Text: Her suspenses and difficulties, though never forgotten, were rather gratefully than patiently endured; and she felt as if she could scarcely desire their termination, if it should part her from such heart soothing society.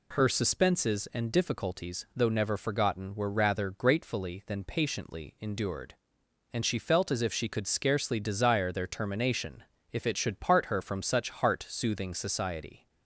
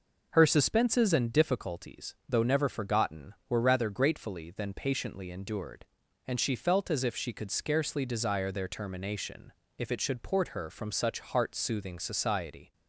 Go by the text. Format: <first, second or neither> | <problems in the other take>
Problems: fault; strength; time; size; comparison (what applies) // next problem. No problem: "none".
first | says "port" for "part"; at 10.2 s